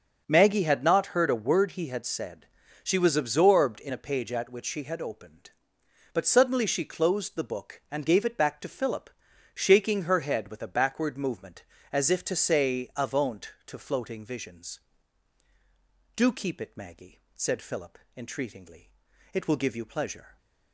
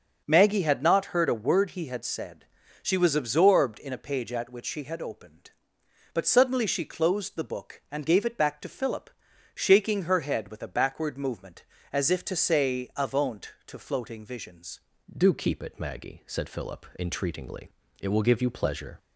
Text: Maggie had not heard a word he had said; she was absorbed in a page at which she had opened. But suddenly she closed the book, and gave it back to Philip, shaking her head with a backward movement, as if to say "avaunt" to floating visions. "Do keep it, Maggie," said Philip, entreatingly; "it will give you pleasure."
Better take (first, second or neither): first